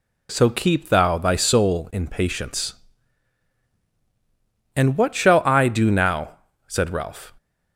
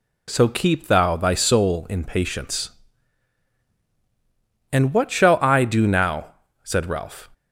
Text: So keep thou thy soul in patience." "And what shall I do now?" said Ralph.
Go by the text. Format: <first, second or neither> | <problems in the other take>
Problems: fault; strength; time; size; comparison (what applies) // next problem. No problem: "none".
neither | none